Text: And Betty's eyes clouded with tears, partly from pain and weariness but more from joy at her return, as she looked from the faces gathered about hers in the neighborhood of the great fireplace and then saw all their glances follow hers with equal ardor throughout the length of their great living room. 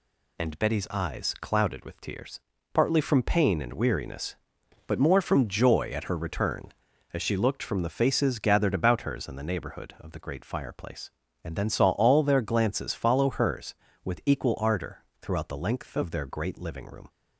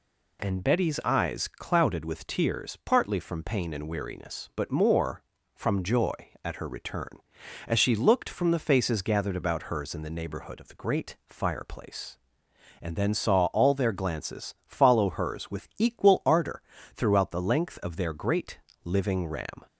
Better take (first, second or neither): first